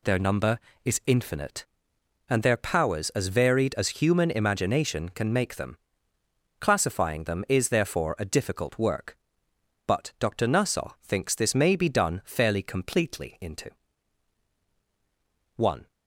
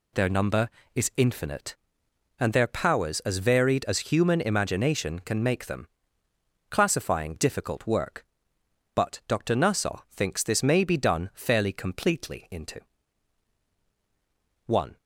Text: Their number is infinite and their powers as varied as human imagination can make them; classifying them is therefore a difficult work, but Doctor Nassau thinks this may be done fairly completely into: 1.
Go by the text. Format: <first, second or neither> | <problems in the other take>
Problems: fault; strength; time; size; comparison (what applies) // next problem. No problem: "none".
first | skips "them is therefore a"; at 7.3 s